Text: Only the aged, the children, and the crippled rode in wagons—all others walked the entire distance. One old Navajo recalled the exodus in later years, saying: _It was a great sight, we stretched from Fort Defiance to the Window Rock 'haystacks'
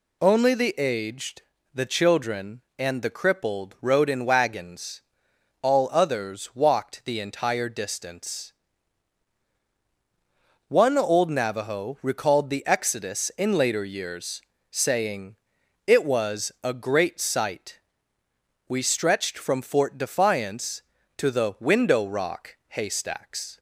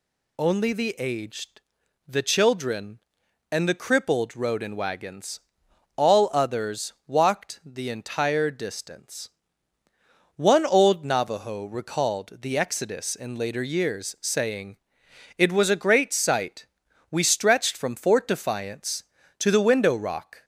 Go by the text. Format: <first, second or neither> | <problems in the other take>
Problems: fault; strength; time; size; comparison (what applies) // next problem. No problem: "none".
first | stops before "haystacks"; at 20.4 s